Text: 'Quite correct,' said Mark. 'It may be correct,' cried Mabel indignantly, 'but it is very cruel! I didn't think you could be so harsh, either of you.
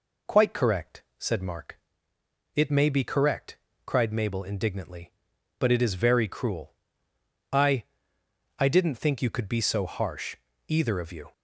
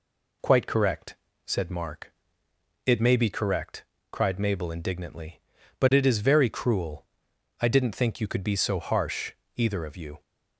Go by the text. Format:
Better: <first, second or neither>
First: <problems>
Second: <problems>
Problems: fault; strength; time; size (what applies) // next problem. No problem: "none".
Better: second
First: says "I" twice; at 8.5 s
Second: none